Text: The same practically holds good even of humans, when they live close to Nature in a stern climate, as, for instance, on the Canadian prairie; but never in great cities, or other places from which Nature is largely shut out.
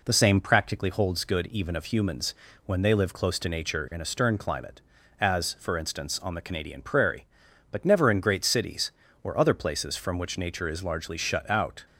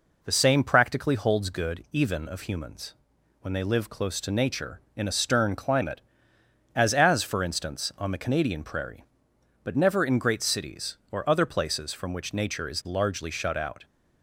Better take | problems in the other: first | says "as" twice; at 6.9 s

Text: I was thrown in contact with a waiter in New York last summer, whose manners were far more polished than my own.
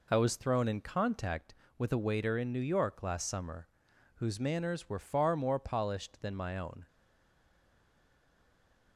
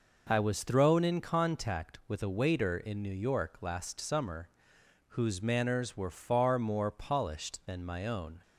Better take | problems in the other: second | stays silent after the last word; noticeable; from 6.8 s on; 2.1 s long

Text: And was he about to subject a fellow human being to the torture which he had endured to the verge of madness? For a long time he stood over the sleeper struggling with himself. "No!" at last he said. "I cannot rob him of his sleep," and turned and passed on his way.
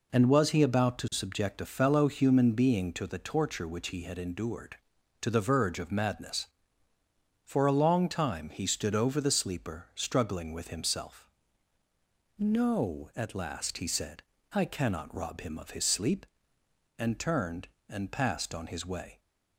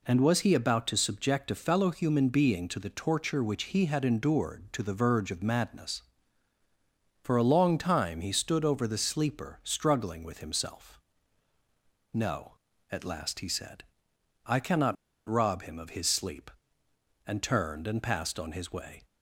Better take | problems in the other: first | pauses between "cannot" and "rob"; slight; at 14.9 s; 0.33 s long

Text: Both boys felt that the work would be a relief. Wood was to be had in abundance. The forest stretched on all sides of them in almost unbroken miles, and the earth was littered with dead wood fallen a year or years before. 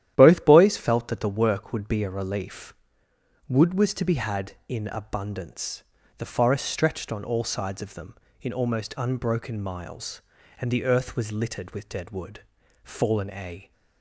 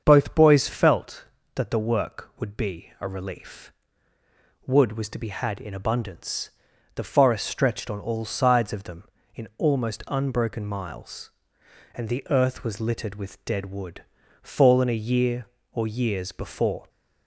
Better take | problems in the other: second | starts louder than the rest; strong; until 1.1 s; 11.5 dB; also in the second // pauses between "wood" and "fallen"; at 12.4 s; 0.42 s long; also in the second // stops before "year or years before"; at 13.7 s

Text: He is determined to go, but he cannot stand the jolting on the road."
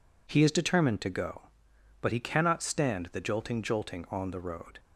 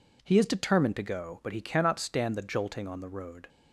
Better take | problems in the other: second | says "jolting" twice; at 3.6 s

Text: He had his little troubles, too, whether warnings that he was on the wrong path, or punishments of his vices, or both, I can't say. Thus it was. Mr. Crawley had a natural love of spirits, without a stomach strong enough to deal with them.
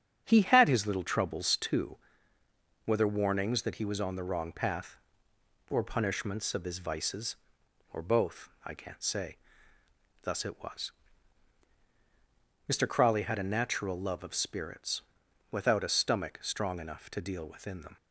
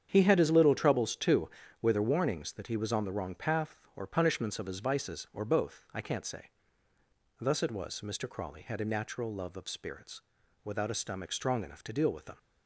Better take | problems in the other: second | starts louder than the rest; strong; until 1.2 s; 7.5 dB; strong in the second // says "within" for "with"; at 17.4 s

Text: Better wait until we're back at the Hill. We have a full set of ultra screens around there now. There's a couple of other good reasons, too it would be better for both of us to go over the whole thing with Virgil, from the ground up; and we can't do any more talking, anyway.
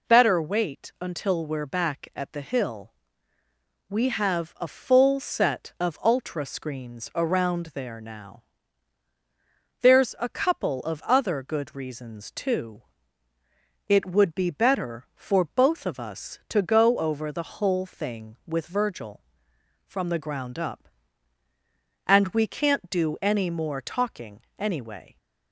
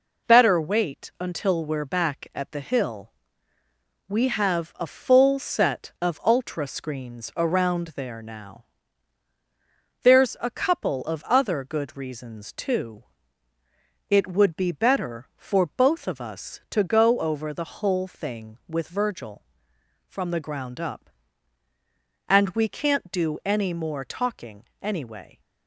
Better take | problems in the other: first | gets quieter; noticeable; throughout; 5 dB // pauses between "too" and "it"; at 13.0 s; 1.0 s long; also in the first

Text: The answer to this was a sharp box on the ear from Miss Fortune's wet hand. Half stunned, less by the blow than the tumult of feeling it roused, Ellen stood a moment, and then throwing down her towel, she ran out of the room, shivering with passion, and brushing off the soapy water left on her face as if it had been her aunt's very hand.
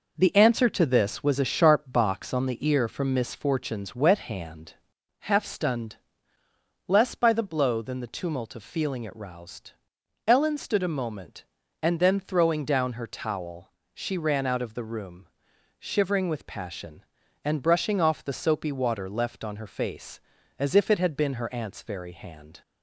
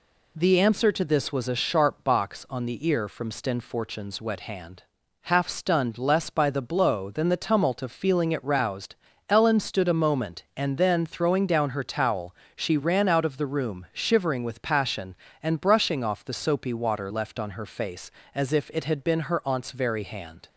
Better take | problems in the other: first | says "Sten" for "Miss"; at 3.2 s

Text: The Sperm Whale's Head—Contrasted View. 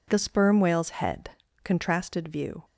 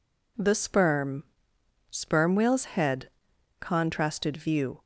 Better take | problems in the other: first | says "Sperm" twice; at 1.9 s

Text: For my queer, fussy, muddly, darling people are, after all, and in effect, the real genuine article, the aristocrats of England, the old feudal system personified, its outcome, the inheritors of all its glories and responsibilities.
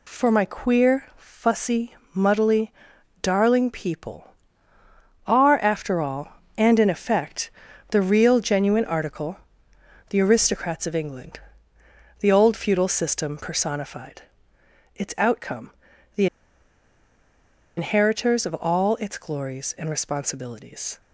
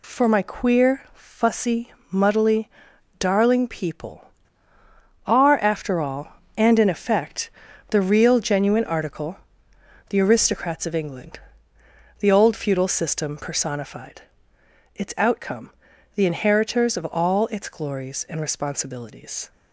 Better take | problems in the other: second | pauses between "the" and "inheritors"; strong; at 16.2 s; 1.5 s long

